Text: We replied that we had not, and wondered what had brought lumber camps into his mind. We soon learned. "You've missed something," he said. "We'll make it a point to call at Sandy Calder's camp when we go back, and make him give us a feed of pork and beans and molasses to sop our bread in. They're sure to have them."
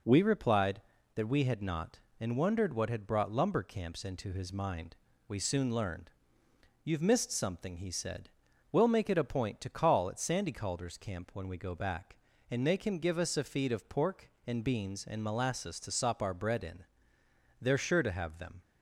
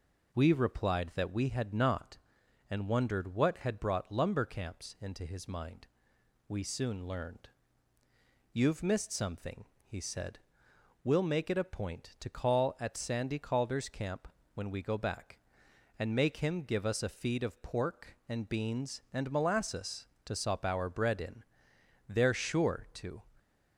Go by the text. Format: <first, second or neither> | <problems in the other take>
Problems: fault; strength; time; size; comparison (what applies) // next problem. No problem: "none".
first | pauses between "camp" and "when"; slight; at 14.2 s; 0.28 s long // stops before "have them"; at 23.3 s